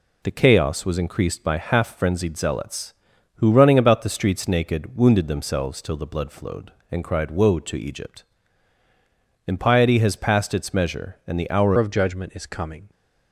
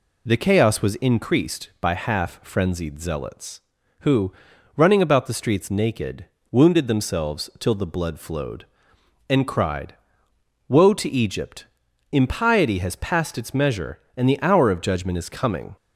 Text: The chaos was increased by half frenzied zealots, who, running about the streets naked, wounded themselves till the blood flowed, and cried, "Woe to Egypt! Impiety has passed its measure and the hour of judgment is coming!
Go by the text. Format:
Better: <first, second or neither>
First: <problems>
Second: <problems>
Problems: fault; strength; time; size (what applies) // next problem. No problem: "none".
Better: second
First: changes voice at "of"; from 11.7 s on; 1.2 s long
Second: none